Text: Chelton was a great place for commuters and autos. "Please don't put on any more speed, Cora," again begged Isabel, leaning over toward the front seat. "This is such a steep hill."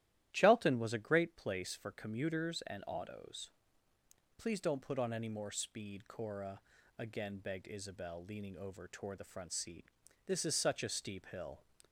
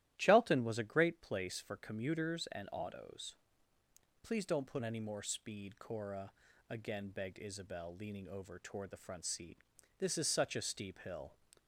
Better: first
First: starts louder than the rest; strong; until 1.3 s; 13 dB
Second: starts louder than the rest; strong; until 1.1 s; 14 dB // skips "on"; at 4.8 s

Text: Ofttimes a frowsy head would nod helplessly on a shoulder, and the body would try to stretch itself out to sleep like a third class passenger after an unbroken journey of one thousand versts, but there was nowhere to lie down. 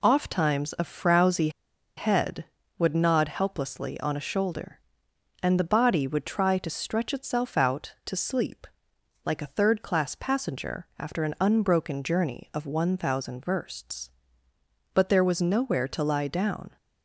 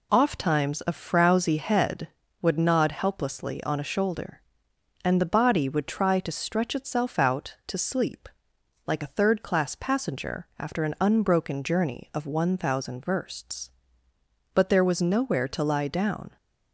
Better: second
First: pauses between "frowsy" and "head"; noticeable; at 1.4 s; 0.47 s long // pauses between "sleep" and "like"; noticeable; at 8.6 s; 0.60 s long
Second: pauses between "sleep" and "like"; noticeable; at 8.2 s; 0.60 s long

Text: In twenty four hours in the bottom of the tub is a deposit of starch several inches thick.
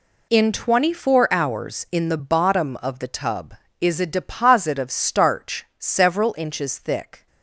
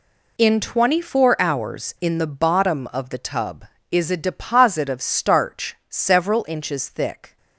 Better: neither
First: none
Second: none

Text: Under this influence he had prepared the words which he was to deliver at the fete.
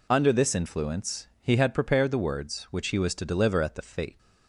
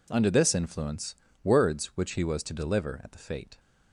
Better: first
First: none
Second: skips "he had prepared the"; at 1.2 s

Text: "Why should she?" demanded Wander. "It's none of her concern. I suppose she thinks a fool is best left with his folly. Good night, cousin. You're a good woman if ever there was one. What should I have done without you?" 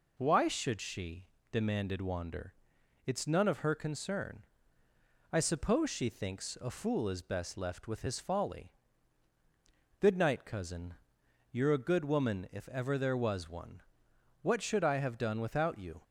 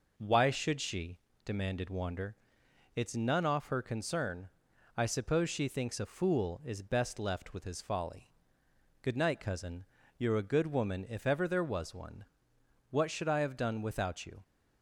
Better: first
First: none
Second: says "off" for "of"; at 3.4 s

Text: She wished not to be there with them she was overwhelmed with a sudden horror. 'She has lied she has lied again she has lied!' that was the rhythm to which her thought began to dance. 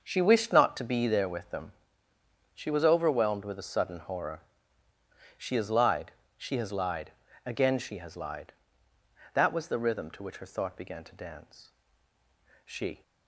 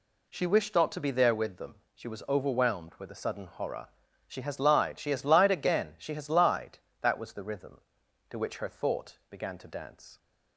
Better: second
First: starts louder than the rest; until 1.0 s; 6.5 dB // pauses between "them" and "she"; noticeable; at 1.7 s; 0.82 s long // pauses between "lied" and "she"; slight; at 6.1 s; 0.24 s long // pauses between "lied" and "again"; slight; at 7.1 s; 0.36 s long // goes on to say "She"; slight; from 12.6 s on; 0.38 s long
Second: pauses between "them" and "she"; slight; at 1.7 s; 0.18 s long

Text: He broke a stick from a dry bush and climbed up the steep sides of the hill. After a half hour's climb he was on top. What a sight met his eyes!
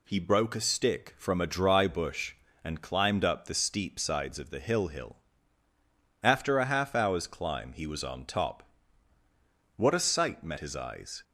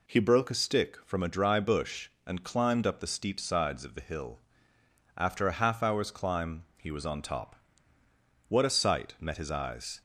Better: second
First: says "hill" twice; at 4.8 s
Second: none

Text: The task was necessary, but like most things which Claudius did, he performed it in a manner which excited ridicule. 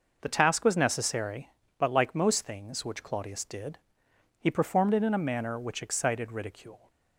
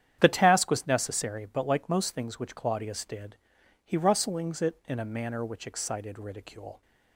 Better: first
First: none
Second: starts louder than the rest; strong; until 1.2 s; 9.5 dB // says "rustlings" for "performed"; at 3.9 s

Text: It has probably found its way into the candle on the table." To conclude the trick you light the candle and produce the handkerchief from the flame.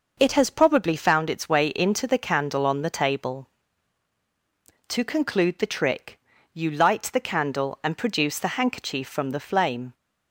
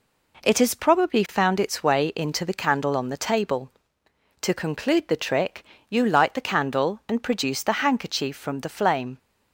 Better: neither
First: pauses between "trick" and "you"; slight; at 6.1 s; 0.36 s long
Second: pauses between "trick" and "you"; slight; at 5.6 s; 0.26 s long

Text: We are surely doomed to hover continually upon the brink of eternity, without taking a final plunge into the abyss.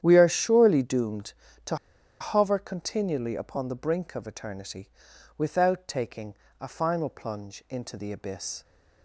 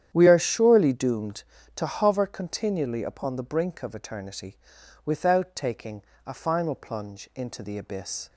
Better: second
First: starts louder than the rest; strong; until 1.0 s; 10 dB // pauses between "to" and "hover"; at 1.7 s; 0.45 s long // pauses between "taking" and "a"; slight; at 6.3 s; 0.24 s long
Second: starts louder than the rest; strong; until 1.1 s; 9.5 dB // pauses between "taking" and "a"; slight; at 6.0 s; 0.22 s long

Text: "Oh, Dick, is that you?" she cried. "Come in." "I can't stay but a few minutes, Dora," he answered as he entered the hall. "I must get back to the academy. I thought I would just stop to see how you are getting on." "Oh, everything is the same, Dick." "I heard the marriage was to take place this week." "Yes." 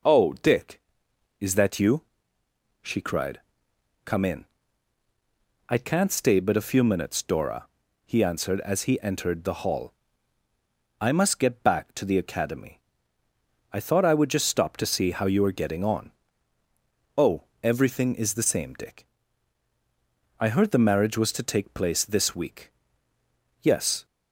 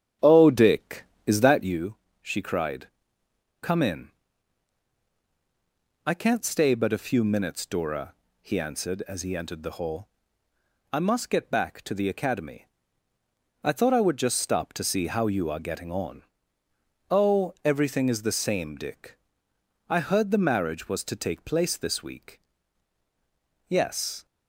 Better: first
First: none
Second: starts louder than the rest; strong; until 1.9 s; 9.5 dB

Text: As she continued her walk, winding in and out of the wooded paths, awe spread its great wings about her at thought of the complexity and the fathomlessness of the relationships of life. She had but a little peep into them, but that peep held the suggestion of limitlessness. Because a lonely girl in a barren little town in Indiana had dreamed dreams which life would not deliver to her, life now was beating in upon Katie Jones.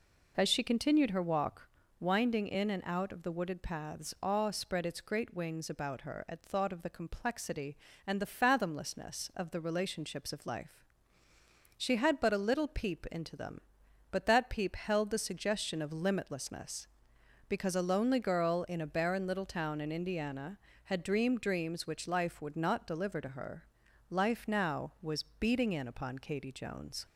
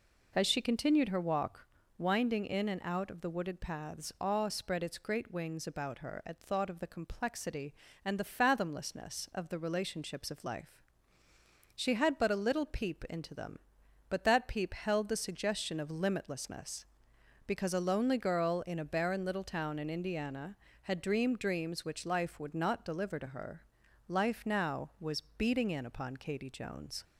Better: neither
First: none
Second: none

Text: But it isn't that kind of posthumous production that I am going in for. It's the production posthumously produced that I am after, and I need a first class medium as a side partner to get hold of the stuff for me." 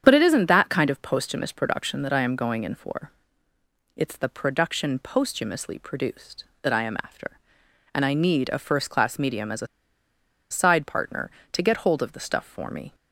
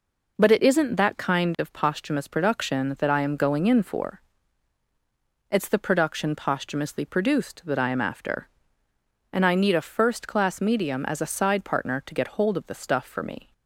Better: second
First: starts louder than the rest; strong; until 1.0 s; 8.5 dB // pauses between "a" and "side"; noticeable; at 9.6 s; 0.83 s long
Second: none

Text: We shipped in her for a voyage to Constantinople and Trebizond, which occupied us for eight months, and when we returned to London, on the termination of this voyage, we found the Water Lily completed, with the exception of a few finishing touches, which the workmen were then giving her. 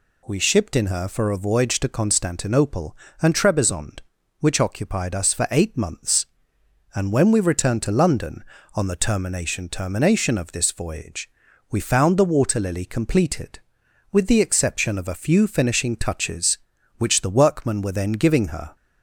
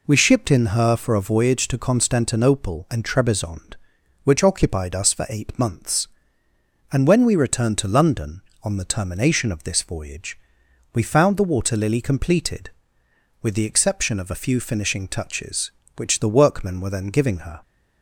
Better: second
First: says "termination" twice; at 9.6 s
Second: none

